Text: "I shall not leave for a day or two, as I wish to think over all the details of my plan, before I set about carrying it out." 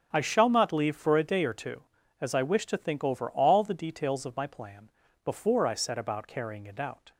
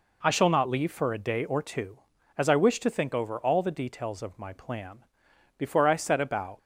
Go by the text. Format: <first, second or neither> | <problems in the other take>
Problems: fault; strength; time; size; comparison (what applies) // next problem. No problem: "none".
first | stops before "carrying it out"; at 6.5 s